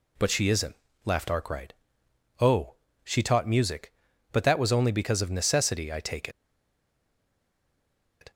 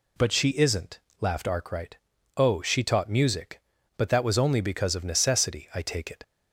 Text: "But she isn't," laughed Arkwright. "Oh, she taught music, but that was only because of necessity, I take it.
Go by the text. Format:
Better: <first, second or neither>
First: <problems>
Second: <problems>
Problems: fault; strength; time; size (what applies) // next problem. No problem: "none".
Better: second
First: pauses between "take" and "it"; strong; at 6.2 s; 1.9 s long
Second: none